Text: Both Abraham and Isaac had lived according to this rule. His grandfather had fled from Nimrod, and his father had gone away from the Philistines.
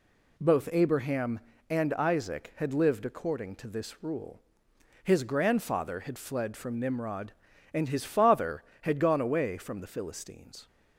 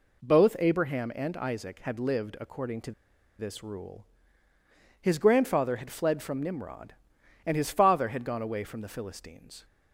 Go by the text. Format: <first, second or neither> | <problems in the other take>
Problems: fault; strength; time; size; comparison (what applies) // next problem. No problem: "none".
first | pauses between "to" and "this"; noticeable; at 2.9 s; 0.46 s long